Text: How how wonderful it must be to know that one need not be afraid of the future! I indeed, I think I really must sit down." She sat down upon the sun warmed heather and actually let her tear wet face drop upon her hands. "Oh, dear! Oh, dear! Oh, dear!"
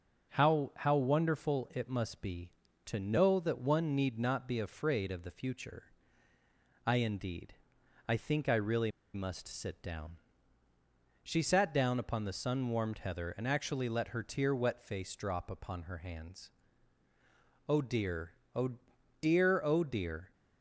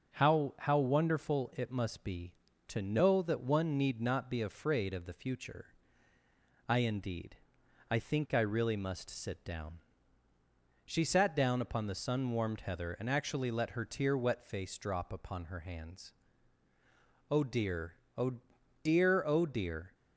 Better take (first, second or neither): second